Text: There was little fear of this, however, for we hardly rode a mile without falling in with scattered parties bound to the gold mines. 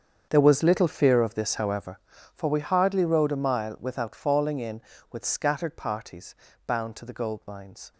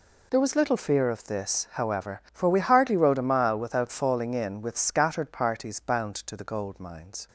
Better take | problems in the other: second | starts louder than the rest; strong; until 2.0 s; 7.5 dB // pauses between "parties" and "bound"; slight; at 6.3 s; 0.32 s long

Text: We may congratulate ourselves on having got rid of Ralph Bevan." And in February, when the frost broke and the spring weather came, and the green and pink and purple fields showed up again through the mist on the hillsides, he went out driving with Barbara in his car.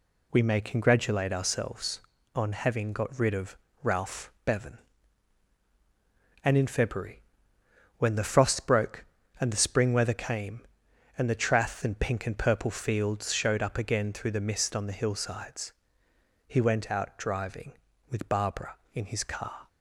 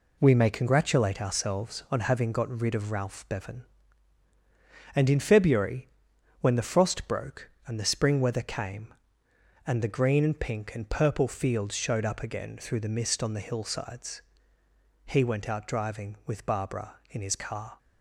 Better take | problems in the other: second | pauses between "of" and "Ralph"; slight; at 3.5 s; 0.26 s long // says "trath" for "green"; at 11.3 s

